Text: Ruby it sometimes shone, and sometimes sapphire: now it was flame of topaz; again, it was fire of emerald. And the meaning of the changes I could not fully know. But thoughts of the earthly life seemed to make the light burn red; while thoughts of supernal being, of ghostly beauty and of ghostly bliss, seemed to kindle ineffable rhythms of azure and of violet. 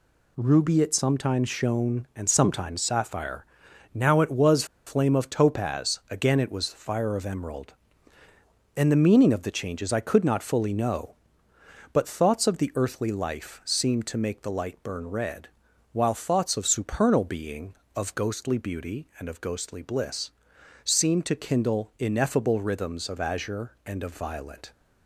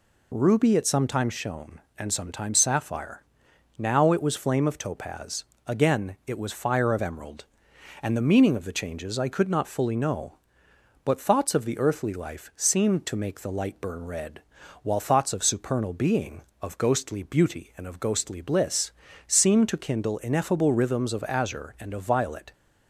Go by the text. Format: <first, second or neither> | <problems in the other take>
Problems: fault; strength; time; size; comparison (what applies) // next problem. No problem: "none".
second | pauses between "was" and "flame"; slight; at 4.6 s; 0.22 s long